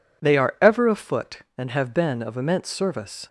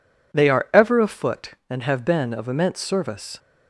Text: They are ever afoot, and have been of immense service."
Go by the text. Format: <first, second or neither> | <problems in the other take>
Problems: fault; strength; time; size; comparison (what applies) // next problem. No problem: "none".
neither | none